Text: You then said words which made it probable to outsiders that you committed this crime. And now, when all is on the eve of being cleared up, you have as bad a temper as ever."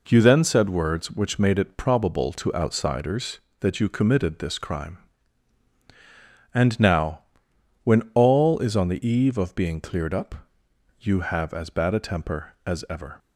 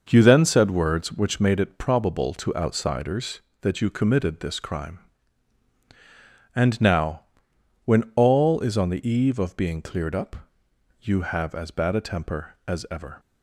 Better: first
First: none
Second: starts louder than the rest; noticeable; until 1.6 s; 6 dB

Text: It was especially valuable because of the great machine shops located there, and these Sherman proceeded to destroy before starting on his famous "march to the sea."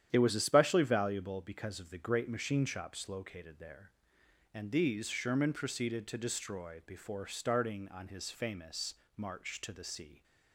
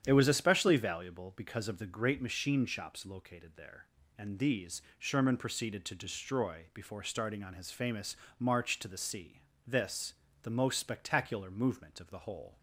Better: first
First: starts louder than the rest; strong; until 1.1 s; 10 dB // pauses between "famous" and "march"; slight; at 8.9 s; 0.20 s long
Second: starts louder than the rest; strong; until 1.0 s; 9 dB // pauses between "these" and "Sherman"; slight; at 4.8 s; 0.16 s long // pauses between "famous" and "march"; slight; at 8.1 s; 0.24 s long // goes on to say "This the most spectacular movement of the whole"; strong; from 9.6 s on; 2.9 s long

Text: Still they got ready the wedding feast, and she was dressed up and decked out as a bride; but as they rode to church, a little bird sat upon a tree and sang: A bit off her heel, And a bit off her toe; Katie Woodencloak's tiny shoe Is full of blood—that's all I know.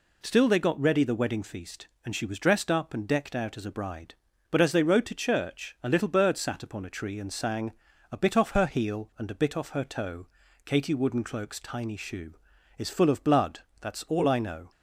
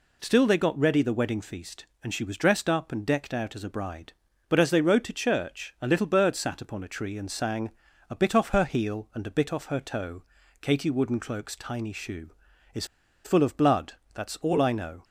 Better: first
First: none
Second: pauses between "Is" and "full"; at 12.8 s; 0.40 s long

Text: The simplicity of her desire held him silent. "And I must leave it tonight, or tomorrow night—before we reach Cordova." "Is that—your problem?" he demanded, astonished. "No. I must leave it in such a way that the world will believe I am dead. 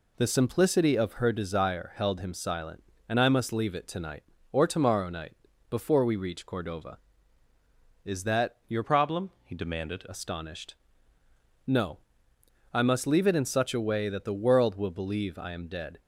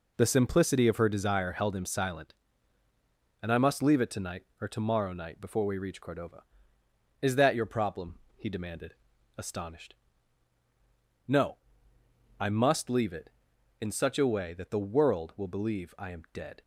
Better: second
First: changes voice from "problem" to "demanded"; from 8.8 to 10.0 s; 1.2 s long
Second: none

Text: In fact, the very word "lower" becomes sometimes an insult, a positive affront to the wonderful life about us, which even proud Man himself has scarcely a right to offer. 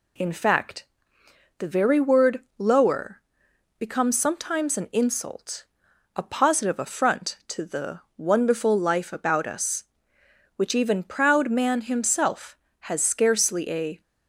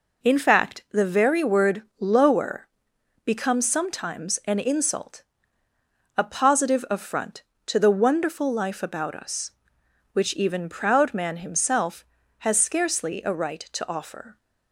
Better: second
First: pauses between "word" and "lower"; slight; at 2.4 s; 0.16 s long // pauses between "lower" and "becomes"; noticeable; at 3.2 s; 0.58 s long // pauses between "the" and "wonderful"; slight; at 8.0 s; 0.16 s long // stops before "right to offer"; at 14.0 s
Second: pauses between "word" and "lower"; slight; at 1.8 s; 0.18 s long // pauses between "lower" and "becomes"; noticeable; at 2.6 s; 0.58 s long

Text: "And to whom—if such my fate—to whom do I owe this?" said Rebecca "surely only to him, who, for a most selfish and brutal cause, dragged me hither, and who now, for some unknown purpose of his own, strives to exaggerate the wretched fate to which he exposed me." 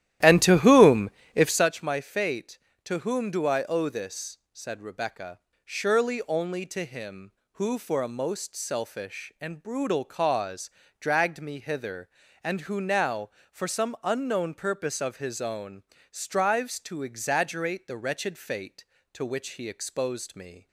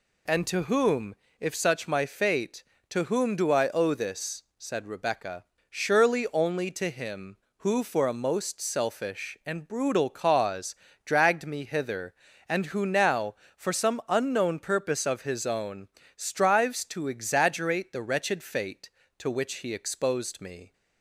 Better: second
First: starts louder than the rest; strong; until 1.7 s; 13 dB // pauses between "Rebecca" and "surely"; slight; at 5.3 s; 0.26 s long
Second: pauses between "Rebecca" and "surely"; slight; at 5.4 s; 0.26 s long

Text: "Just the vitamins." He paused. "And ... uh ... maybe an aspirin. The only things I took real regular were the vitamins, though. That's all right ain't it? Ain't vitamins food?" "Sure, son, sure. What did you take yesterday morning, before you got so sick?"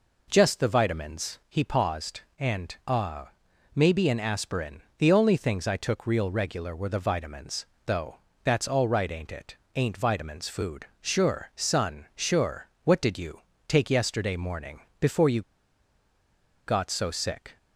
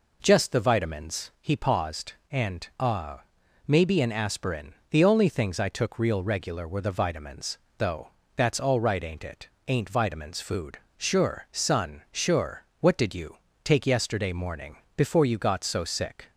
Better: second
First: pauses between "you" and "take"; slight; at 13.3 s; 0.28 s long // pauses between "you" and "got"; strong; at 15.4 s; 1.2 s long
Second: pauses between "you" and "take"; slight; at 13.3 s; 0.28 s long

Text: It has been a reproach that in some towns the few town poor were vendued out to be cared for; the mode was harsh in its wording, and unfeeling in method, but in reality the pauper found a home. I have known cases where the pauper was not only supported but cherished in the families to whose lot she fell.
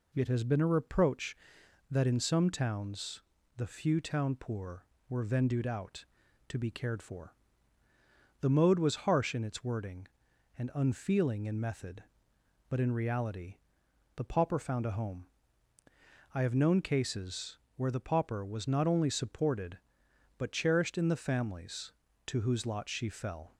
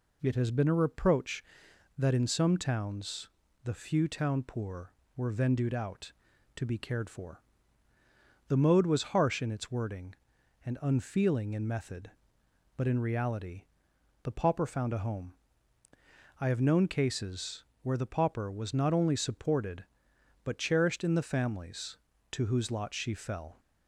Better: neither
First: pauses between "towns" and "the"; slight; at 3.2 s; 0.36 s long // pauses between "reality" and "the"; noticeable; at 13.5 s; 0.60 s long // pauses between "cases" and "where"; slight; at 17.5 s; 0.18 s long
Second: pauses between "towns" and "the"; slight; at 3.2 s; 0.36 s long // pauses between "reality" and "the"; noticeable; at 13.6 s; 0.60 s long // pauses between "cases" and "where"; slight; at 17.6 s; 0.18 s long

